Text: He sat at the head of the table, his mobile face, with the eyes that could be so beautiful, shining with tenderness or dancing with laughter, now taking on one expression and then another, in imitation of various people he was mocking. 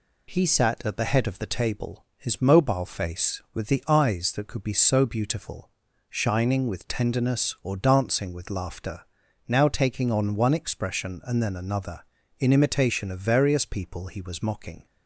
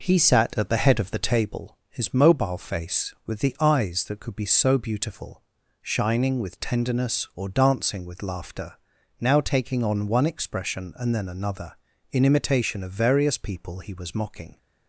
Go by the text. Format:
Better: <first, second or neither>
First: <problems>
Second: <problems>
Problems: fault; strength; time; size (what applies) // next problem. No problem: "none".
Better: first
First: none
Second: starts louder than the rest; noticeable; until 1.6 s; 5 dB